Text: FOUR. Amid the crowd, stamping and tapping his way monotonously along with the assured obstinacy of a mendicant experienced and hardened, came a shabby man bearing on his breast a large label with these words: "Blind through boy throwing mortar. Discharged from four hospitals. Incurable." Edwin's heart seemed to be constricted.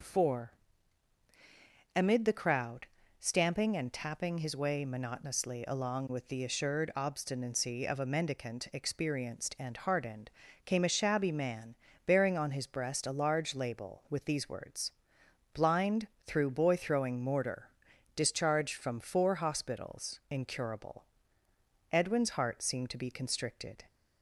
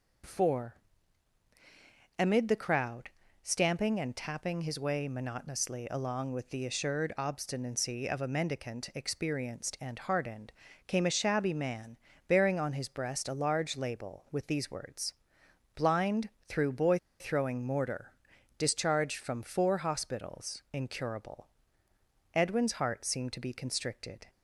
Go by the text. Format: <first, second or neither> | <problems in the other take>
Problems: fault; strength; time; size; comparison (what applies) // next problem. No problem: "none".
first | pauses between "man" and "bearing"; slight; at 11.9 s; 0.30 s long; slight in the first // pauses between "Blind" and "through"; slight; at 16.3 s; 0.18 s long; slight in the first // pauses between "boy" and "throwing"; slight; at 16.9 s; 0.23 s long